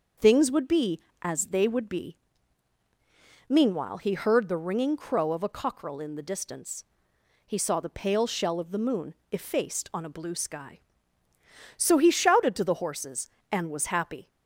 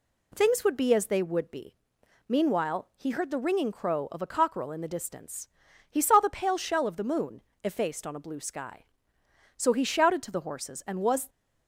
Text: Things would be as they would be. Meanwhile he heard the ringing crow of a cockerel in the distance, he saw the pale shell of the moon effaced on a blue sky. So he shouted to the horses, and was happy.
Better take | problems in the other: first | pauses between "moon" and "effaced"; slight; at 7.4 s; 0.22 s long; slight in the first // stops before "happy"; at 11.2 s

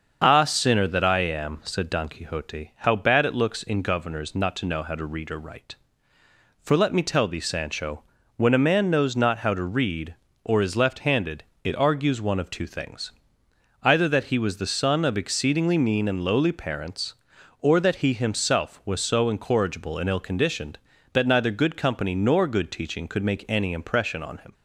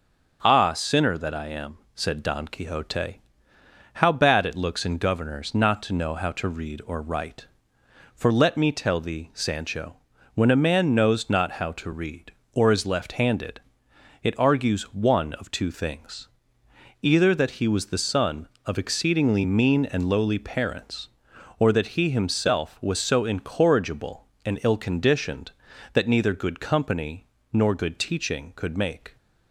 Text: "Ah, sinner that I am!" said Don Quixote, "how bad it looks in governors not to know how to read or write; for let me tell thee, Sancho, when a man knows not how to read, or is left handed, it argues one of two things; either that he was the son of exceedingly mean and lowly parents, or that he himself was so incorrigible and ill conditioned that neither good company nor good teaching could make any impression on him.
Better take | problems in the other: first | starts louder than the rest; noticeable; until 1.4 s; 6 dB; also in the first // pauses between "company" and "nor"; slight; at 27.2 s; 0.24 s long // stops before "any impression on him"; at 29.1 s

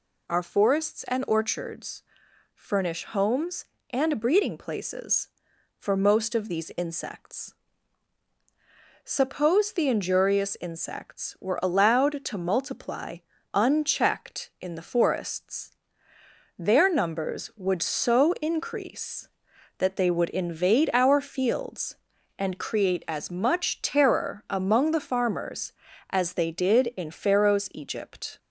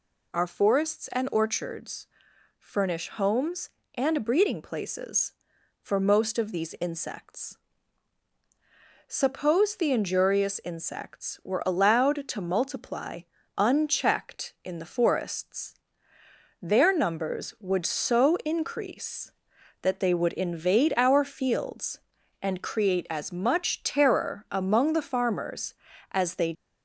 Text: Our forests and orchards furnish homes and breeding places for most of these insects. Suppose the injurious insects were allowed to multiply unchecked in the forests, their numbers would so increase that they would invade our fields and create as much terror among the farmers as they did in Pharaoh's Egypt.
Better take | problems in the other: first | pauses between "orchards" and "furnish"; noticeable; at 2.0 s; 0.54 s long; noticeable in the first // pauses between "multiply" and "unchecked"; slight; at 13.2 s; 0.36 s long; slight in the first // stops before "did in Pharaoh's Egypt"; at 26.5 s

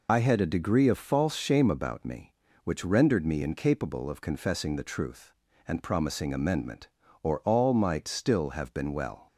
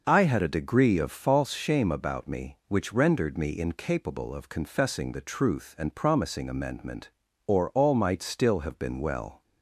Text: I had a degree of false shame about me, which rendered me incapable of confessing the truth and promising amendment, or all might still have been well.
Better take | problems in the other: second | loses the start of "I"; at 0.0 s; 70 ms

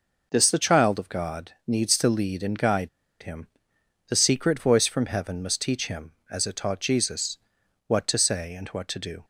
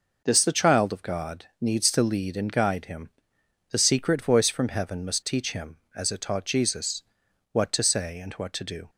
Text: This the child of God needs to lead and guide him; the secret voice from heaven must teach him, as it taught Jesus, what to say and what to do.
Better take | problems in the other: second | pauses between "God" and "needs"; slight; at 1.5 s; 0.16 s long; slight in the second // pauses between "guide" and "him"; slight; at 2.8 s; 0.33 s long

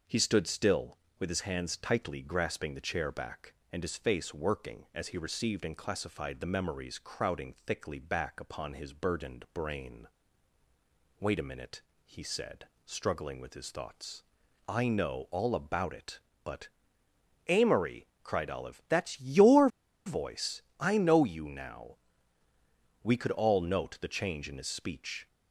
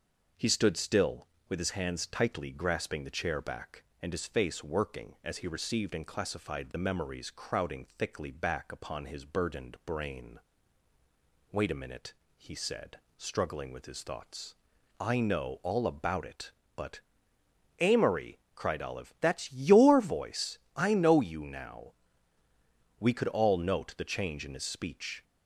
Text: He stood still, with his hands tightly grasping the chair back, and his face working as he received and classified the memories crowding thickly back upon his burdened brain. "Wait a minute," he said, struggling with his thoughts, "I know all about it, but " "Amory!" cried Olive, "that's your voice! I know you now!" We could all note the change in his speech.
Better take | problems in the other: second | pauses between "your" and "voice"; at 19.6 s; 0.38 s long

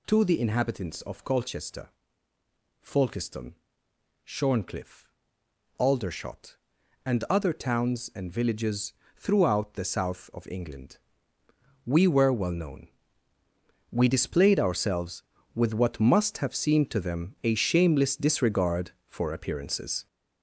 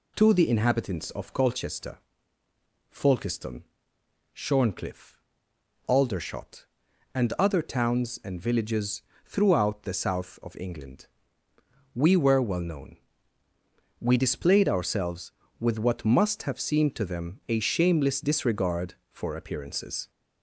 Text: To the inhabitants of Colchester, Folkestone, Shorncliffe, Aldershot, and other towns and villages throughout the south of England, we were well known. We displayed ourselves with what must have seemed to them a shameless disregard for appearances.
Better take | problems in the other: second | gets louder; noticeable; throughout; 5.5 dB // pauses between "villages" and "throughout"; slight; at 8.9 s; 0.22 s long; slight in the second

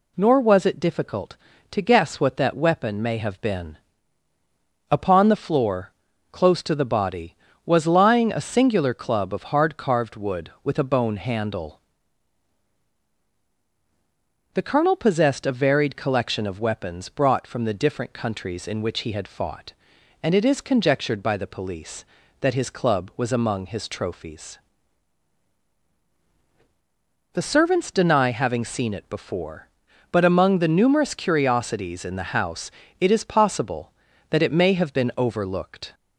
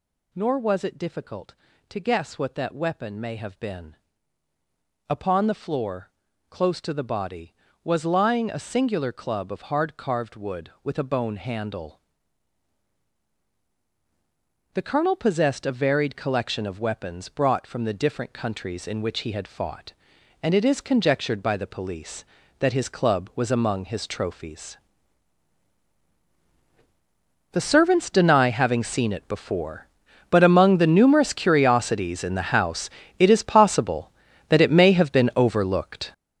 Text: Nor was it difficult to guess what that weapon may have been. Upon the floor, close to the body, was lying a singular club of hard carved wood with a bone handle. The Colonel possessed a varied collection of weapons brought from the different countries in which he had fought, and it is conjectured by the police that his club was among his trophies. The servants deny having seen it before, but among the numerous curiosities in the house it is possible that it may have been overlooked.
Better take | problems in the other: first | gets louder; strong; throughout; 10.5 dB // pauses between "house" and "it"; slight; at 32.8 s; 0.30 s long; slight in the first

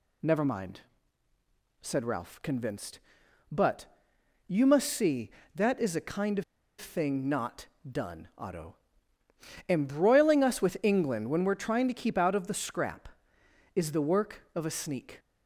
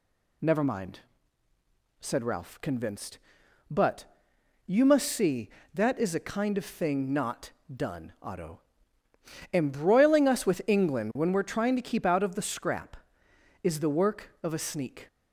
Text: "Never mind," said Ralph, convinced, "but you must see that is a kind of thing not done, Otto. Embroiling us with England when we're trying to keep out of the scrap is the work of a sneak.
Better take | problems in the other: second | pauses between "but" and "you"; noticeable; at 3.8 s; 0.60 s long; noticeable in the second // pauses between "of" and "thing"; slight; at 6.4 s; 0.35 s long // pauses between "not" and "done"; slight; at 7.6 s; 0.22 s long; slight in the second

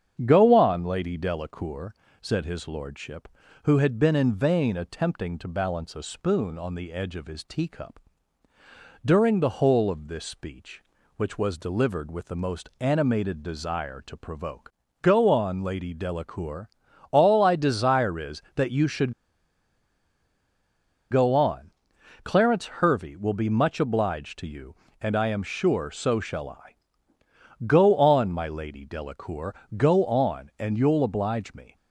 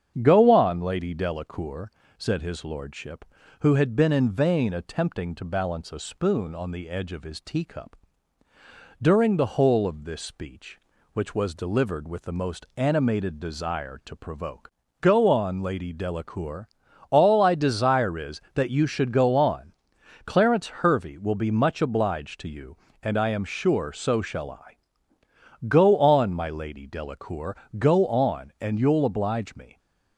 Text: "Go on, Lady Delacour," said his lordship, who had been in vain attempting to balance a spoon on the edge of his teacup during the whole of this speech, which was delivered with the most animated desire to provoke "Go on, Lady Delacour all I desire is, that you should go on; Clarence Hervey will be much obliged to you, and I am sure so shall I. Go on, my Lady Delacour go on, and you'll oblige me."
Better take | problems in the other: second | starts louder than the rest; strong; until 1.2 s; 8 dB; strong in the second // pauses between "teacup" and "during"; at 7.9 s; 1.0 s long; also in the second // pauses between "provoke" and "Go"; slight; at 14.7 s; 0.30 s long; slight in the second // pauses between "Delacour" and "all"; at 16.6 s; 0.42 s long; also in the second // pauses between "should" and "go"; strong; at 19.1 s; 1.9 s long // pauses between "Delacour" and "go"; slight; at 29.5 s; 0.24 s long; slight in the second

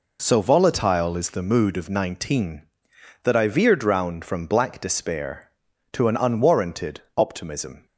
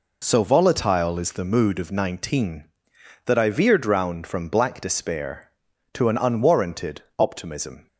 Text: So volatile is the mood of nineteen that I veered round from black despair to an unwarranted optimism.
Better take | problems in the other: neither | pauses between "unwarranted" and "optimism"; slight; the same in both

